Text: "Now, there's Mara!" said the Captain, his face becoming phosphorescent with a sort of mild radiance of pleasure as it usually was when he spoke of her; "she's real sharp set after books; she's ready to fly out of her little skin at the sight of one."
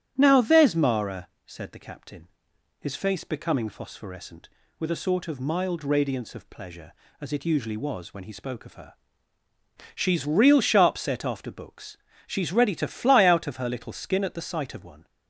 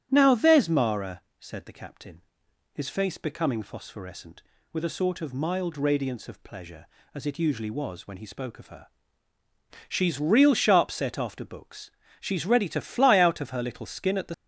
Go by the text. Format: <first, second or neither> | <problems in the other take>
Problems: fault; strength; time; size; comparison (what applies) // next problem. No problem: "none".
first | starts louder than the rest; strong; until 1.1 s; 10.5 dB; strong in the first // stops before "sight of one"; at 14.3 s